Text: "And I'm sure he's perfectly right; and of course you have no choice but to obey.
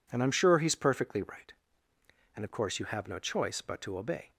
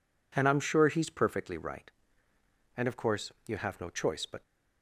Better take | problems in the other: first | stops before "to obey"; at 4.4 s

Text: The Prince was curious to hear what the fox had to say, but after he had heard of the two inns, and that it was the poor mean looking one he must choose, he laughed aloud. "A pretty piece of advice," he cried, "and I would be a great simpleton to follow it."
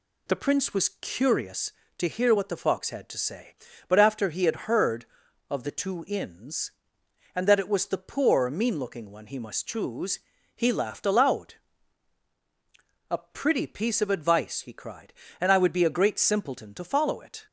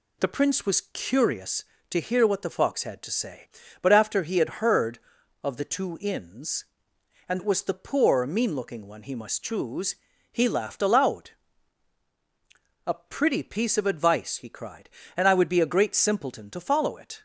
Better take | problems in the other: first | skips "that"; at 7.3 s

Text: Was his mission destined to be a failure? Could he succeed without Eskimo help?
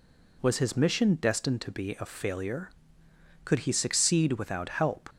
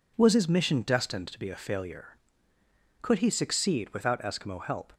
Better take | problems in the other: second | skips "Eskimo"; at 4.6 s

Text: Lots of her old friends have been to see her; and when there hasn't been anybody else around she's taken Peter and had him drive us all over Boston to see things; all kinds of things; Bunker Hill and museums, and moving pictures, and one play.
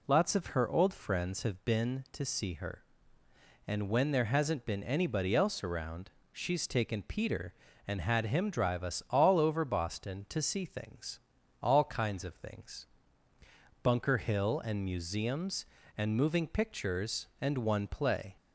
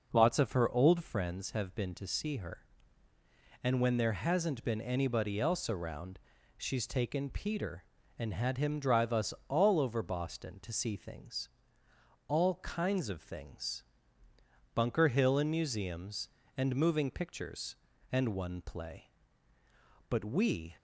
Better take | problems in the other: first | pauses between "around" and "she's"; at 6.1 s; 0.38 s long; slight in the first // goes on to say "But we"; noticeable; from 20.0 s on; 0.66 s long

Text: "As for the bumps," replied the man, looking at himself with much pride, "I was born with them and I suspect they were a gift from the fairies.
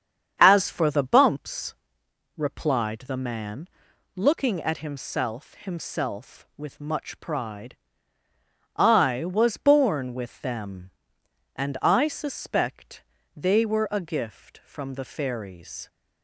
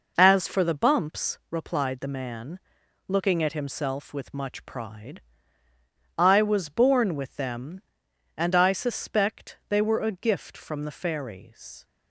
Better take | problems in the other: second | starts louder than the rest; strong; until 1.3 s; 8 dB // says "himself" twice; at 5.5 s // pauses between "suspect" and "they"; slight; at 13.0 s; 0.32 s long

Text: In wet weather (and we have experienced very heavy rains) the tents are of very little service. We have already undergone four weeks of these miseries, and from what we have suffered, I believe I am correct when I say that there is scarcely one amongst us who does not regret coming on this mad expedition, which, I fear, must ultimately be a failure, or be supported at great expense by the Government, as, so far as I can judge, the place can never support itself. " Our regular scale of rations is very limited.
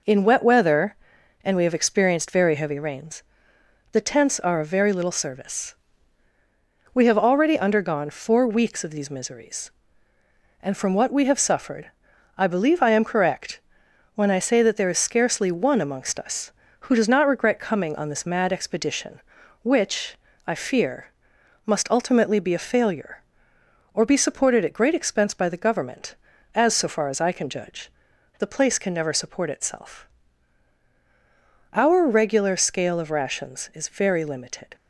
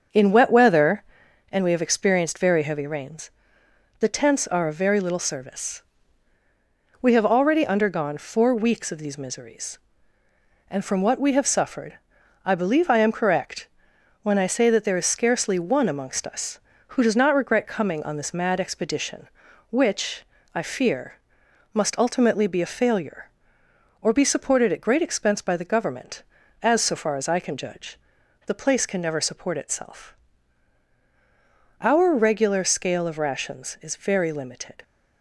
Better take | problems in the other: first | starts louder than the rest; until 1.4 s; 7 dB // pauses between "correct" and "when"; noticeable; at 13.6 s; 0.54 s long; noticeable in the first

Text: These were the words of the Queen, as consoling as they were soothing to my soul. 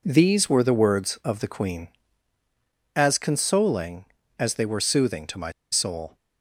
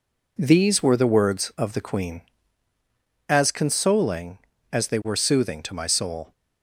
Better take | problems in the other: second | pauses between "my" and "soul"; slight; at 5.5 s; 0.21 s long

